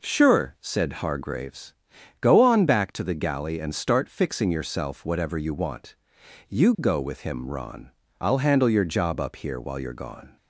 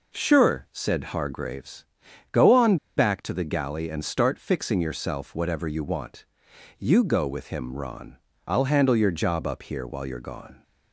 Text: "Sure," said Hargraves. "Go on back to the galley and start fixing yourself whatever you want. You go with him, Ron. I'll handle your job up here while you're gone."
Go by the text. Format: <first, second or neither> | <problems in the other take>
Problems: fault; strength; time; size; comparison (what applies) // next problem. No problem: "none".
first | pauses between "on" and "back"; slight; at 2.7 s; 0.21 s long